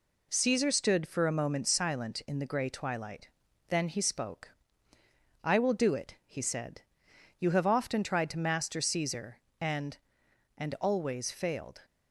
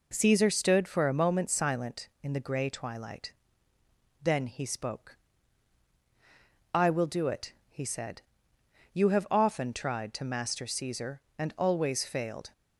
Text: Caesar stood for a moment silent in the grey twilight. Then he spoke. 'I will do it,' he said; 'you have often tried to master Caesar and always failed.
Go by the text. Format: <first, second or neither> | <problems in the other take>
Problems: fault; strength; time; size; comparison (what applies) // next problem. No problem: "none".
second | says "and" twice; at 10.5 s